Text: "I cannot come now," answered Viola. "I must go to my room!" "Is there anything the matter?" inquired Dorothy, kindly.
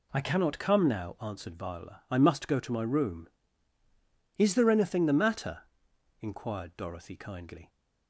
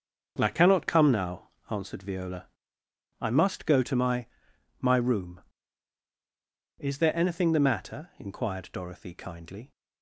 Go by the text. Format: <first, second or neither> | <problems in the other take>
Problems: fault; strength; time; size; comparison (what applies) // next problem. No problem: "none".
first | starts louder than the rest; until 1.3 s; 6.5 dB // says "my" twice; at 4.7 s